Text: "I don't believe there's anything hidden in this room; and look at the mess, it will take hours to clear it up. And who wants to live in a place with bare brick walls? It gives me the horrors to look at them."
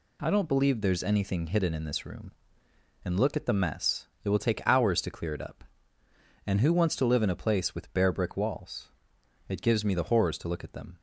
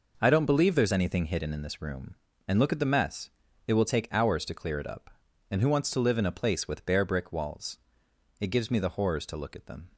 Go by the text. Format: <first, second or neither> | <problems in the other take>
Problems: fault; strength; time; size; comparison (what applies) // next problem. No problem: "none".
neither | none